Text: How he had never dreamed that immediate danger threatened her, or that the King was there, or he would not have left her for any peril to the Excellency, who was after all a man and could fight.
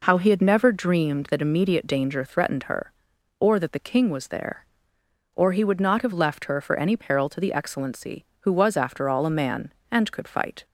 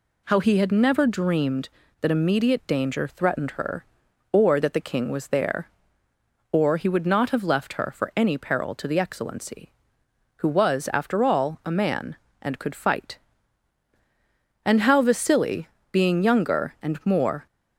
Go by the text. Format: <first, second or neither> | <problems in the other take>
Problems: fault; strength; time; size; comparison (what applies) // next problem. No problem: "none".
first | goes on to say "And How Vasili being younger and more"; strong; from 14.6 s on; 2.8 s long